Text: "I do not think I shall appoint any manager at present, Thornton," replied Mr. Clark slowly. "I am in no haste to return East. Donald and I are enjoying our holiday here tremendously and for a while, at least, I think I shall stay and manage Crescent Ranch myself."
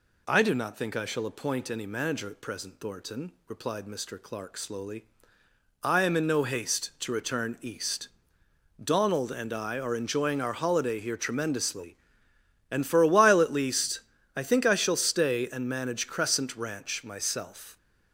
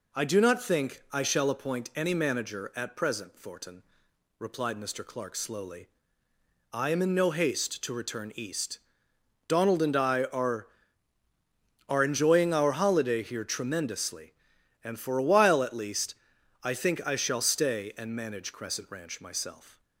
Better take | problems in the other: first | says "are" twice; at 11.8 s

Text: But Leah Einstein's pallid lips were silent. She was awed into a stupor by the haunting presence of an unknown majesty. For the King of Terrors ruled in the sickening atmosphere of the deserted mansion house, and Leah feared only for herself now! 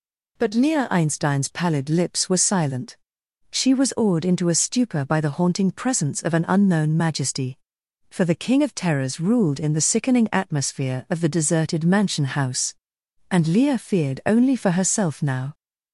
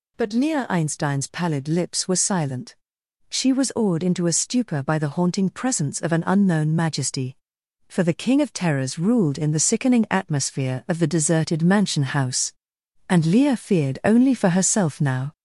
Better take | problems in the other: first | gets louder; noticeable; throughout; 4 dB

